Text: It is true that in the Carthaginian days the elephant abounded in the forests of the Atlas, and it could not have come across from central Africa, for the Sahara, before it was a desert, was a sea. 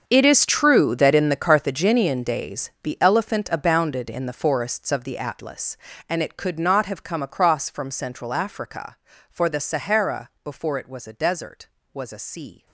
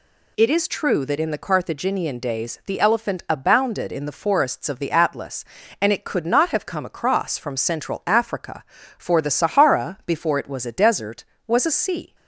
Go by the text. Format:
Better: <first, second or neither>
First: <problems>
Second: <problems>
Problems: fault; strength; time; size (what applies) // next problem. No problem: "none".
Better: second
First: gets quieter; strong; throughout; 17 dB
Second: none